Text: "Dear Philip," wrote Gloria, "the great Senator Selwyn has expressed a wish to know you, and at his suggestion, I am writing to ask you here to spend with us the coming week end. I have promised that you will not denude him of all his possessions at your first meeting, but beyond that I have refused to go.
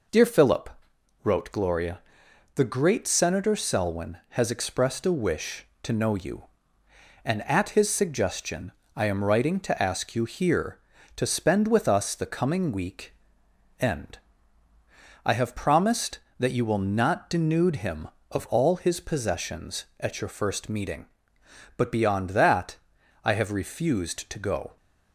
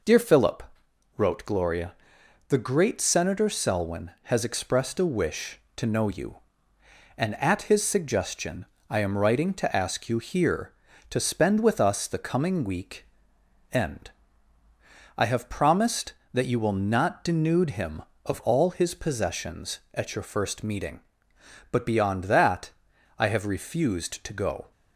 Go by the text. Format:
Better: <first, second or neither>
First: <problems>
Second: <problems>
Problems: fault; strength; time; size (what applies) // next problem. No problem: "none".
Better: neither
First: pauses between "week" and "end"; noticeable; at 13.1 s; 0.68 s long // pauses between "that" and "I"; noticeable; at 22.7 s; 0.48 s long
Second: pauses between "week" and "end"; noticeable; at 13.0 s; 0.68 s long // pauses between "that" and "I"; noticeable; at 22.7 s; 0.48 s long